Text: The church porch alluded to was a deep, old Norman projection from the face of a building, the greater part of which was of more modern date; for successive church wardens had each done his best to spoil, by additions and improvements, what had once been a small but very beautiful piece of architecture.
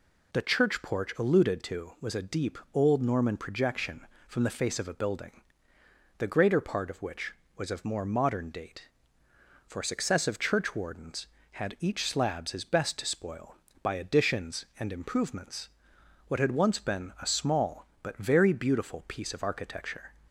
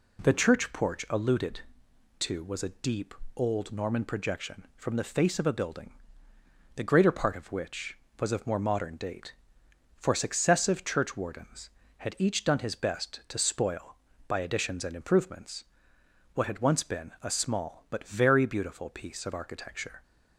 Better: second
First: says "slabs" for "done"; at 12.0 s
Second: none

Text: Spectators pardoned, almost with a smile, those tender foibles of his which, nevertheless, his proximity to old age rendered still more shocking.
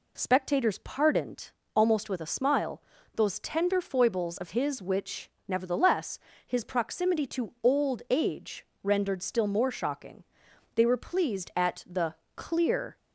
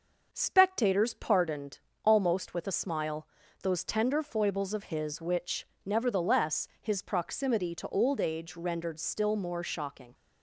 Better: second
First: pauses between "age" and "rendered"; slight; at 8.6 s; 0.20 s long // goes on to say "They were pleased at the clear"; strong; from 10.7 s on; 2.2 s long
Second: none

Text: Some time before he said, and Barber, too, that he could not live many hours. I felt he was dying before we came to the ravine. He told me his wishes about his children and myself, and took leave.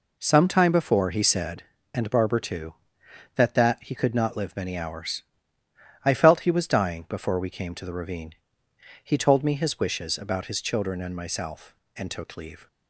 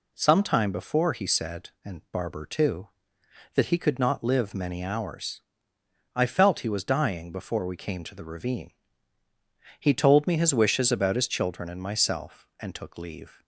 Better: second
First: says "that" twice; at 3.5 s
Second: none

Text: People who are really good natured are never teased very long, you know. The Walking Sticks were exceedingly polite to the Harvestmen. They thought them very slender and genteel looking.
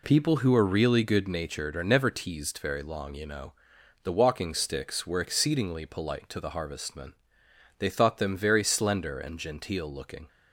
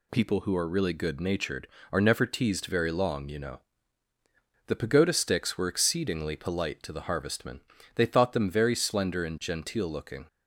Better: first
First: none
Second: says "Pagoda" for "Walking"; at 4.7 s

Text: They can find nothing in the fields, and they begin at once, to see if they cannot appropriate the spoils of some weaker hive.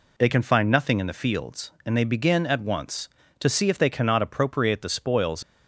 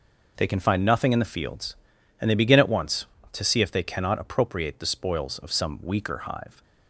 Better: second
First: stops before "of some weaker hive"; at 5.4 s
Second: none

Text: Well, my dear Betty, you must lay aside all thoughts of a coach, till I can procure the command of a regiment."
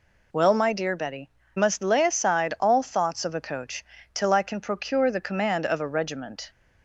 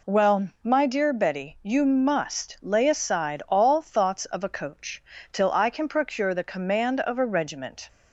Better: second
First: skips "you"; at 1.4 s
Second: none

